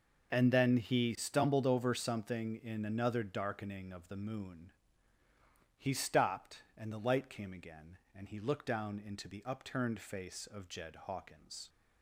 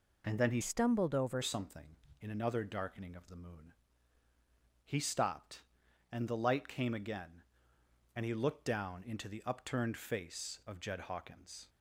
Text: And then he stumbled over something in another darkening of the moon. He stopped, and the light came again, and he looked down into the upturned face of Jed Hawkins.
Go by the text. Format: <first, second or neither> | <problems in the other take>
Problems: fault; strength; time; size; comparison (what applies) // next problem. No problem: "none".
first | changes voice from "stumbled" to "over"; from 0.6 to 1.4 s; 0.8 s long